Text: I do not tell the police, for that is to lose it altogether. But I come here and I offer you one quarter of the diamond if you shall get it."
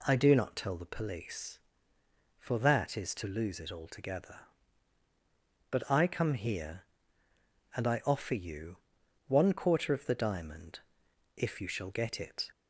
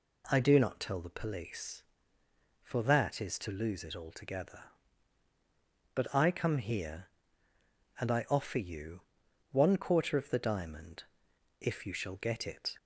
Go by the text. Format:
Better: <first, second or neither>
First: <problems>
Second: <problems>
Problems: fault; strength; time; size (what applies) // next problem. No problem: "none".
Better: neither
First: pauses between "you" and "one"; noticeable; at 8.7 s; 0.50 s long // pauses between "diamond" and "if"; noticeable; at 10.7 s; 0.56 s long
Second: pauses between "you" and "one"; noticeable; at 9.0 s; 0.50 s long // pauses between "diamond" and "if"; noticeable; at 11.0 s; 0.56 s long